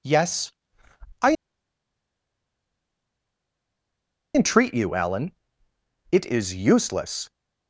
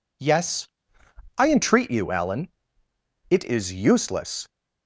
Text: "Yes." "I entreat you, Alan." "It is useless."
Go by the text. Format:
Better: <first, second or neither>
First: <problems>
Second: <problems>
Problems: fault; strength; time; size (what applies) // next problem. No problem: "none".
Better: second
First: pauses between "I" and "entreat"; strong; at 1.3 s; 2.9 s long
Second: none